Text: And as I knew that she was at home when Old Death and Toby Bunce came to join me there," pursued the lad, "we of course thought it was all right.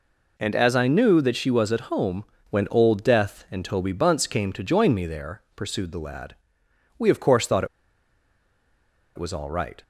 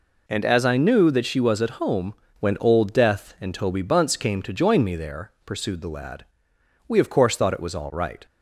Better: second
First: pauses between "home" and "when"; slight; at 2.2 s; 0.26 s long // pauses between "thought" and "it"; strong; at 7.6 s; 1.5 s long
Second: pauses between "home" and "when"; slight; at 2.1 s; 0.26 s long

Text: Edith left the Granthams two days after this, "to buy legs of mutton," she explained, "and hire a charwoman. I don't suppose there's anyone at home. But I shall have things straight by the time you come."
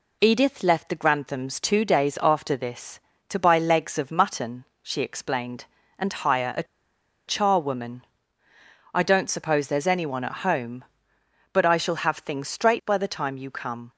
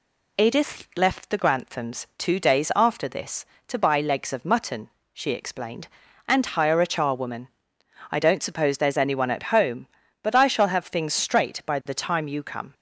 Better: second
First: pauses between "a" and "charwoman"; noticeable; at 6.6 s; 0.63 s long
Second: none

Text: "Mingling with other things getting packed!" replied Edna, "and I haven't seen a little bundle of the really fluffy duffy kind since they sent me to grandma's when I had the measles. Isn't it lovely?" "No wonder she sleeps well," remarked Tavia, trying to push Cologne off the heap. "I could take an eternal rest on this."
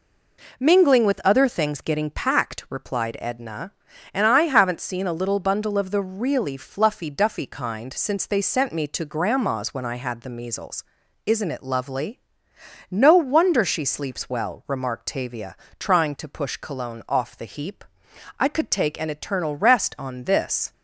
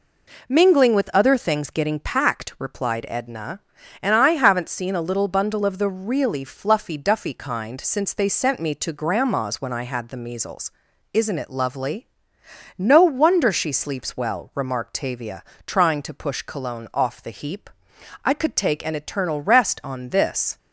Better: neither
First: none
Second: none

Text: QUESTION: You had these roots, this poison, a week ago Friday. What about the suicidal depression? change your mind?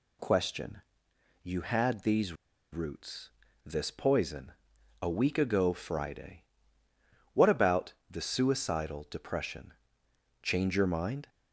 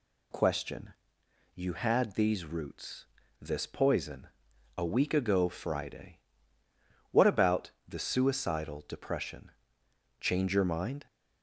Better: second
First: pauses between "these" and "roots"; at 2.3 s; 0.38 s long // pauses between "about" and "the"; slight; at 7.9 s; 0.16 s long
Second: pauses between "about" and "the"; slight; at 7.7 s; 0.16 s long

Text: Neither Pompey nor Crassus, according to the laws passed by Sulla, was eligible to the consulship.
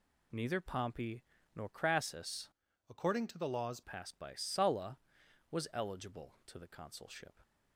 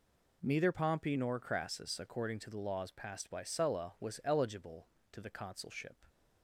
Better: second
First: pauses between "Pompey" and "nor"; slight; at 1.2 s; 0.30 s long // changes voice from "according" to "laws"; from 2.8 to 3.8 s; 1.0 s long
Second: none

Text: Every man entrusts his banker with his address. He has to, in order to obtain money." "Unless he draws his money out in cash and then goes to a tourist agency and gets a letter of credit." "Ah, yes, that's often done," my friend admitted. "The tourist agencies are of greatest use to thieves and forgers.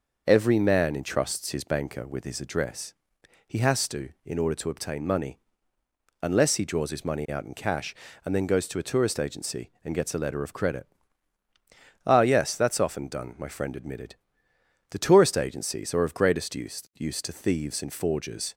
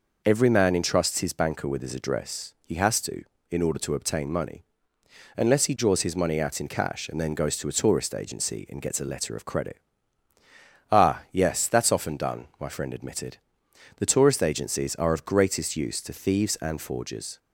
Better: second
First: says "use" twice; at 16.9 s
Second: none

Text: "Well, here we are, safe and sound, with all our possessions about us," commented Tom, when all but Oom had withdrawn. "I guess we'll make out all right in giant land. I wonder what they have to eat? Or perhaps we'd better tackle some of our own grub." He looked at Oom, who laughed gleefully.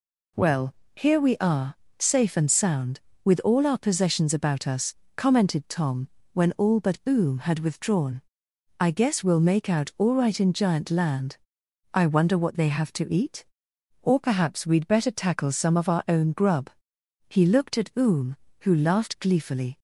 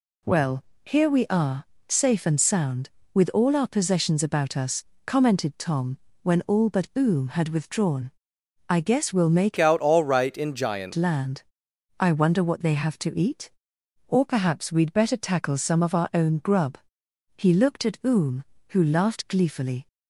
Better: first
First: none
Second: changes voice from "out" to "giant"; from 9.5 to 10.9 s; 1.4 s long

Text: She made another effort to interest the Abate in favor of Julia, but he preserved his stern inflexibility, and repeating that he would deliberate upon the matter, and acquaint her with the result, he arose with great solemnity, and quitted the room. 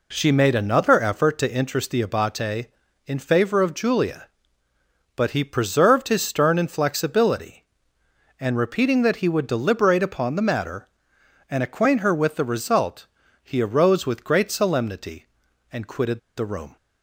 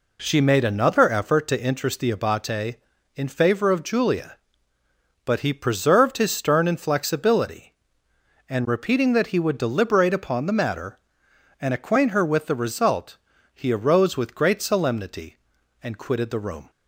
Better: second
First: pauses between "quitted" and "the"; slight; at 16.1 s; 0.17 s long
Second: none

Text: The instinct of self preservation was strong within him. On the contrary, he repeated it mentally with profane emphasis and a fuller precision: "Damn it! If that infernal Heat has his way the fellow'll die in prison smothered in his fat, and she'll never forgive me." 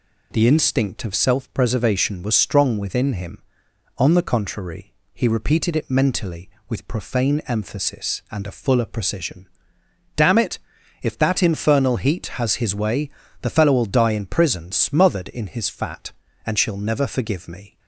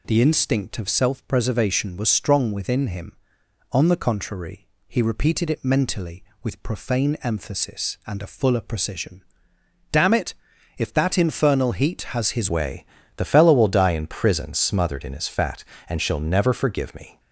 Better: first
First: pauses between "way" and "the"; slight; at 13.1 s; 0.30 s long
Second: changes voice at "way"; from 12.4 s on; 4.7 s long // pauses between "way" and "the"; slight; at 12.8 s; 0.32 s long

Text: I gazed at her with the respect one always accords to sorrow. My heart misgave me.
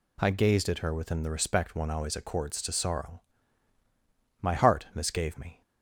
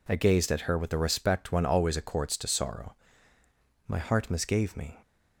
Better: second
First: says "within" for "with"; at 0.9 s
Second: none

